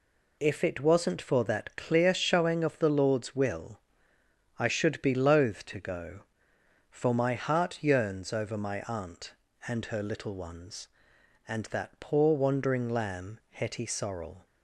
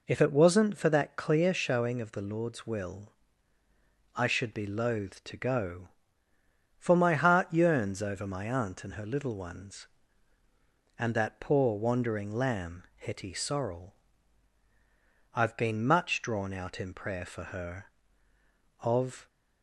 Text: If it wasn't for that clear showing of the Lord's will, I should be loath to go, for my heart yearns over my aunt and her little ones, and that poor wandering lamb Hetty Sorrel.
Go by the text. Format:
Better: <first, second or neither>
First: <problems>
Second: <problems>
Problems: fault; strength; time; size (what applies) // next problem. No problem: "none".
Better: first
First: none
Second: goes on to say "I've been much drawn out in prayer for her of"; strong; from 15.3 s on; 3.9 s long